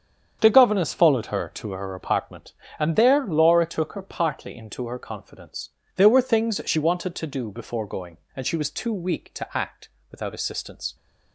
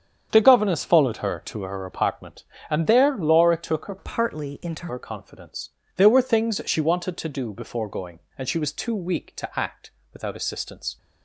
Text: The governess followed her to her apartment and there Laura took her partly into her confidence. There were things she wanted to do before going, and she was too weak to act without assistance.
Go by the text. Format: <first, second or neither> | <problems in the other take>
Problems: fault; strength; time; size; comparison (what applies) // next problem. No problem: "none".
first | starts louder than the rest; strong; until 1.3 s; 7.5 dB; strong in the first // changes voice from "partly" to "into"; from 3.9 to 4.8 s; 0.9 s long // pauses between "act" and "without"; slight; at 9.8 s; 0.24 s long; slight in the first